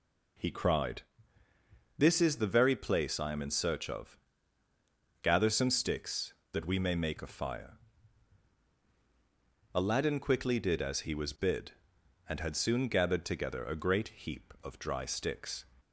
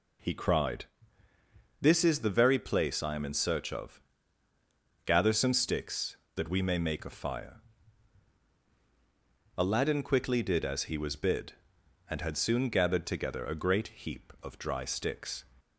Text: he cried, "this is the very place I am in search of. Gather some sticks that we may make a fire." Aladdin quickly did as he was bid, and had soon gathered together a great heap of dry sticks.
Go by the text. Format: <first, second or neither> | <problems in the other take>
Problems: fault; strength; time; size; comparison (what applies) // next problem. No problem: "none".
neither | none